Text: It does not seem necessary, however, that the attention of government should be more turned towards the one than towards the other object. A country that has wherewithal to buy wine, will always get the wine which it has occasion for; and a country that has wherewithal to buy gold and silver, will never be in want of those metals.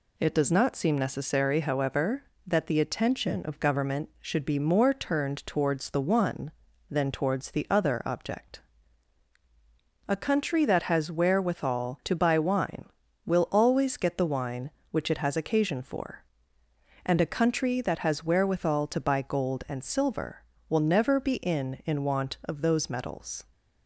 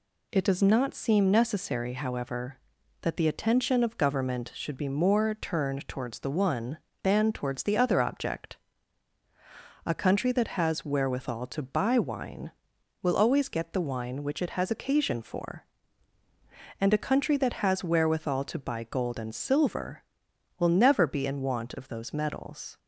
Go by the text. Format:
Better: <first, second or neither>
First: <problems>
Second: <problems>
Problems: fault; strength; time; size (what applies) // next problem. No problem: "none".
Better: second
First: says "in" twice; at 21.8 s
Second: none